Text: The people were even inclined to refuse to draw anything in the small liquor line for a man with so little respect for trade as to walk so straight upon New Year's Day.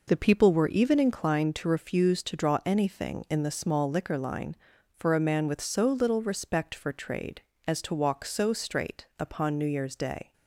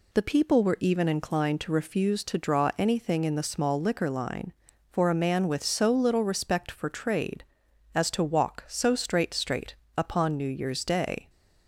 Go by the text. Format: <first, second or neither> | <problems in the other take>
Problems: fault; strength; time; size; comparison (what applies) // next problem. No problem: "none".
first | says "straight" twice; at 9.3 s